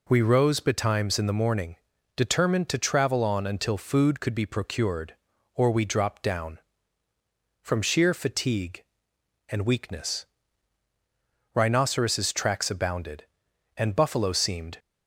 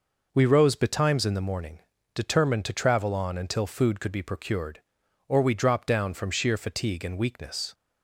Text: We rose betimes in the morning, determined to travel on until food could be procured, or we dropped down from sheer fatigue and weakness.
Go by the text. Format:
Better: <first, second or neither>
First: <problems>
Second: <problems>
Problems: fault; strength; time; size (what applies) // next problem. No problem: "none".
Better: second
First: goes on to say "Rhinoceros tracks abounded and buffalo seemed"; strong; from 11.5 s on; 3.2 s long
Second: none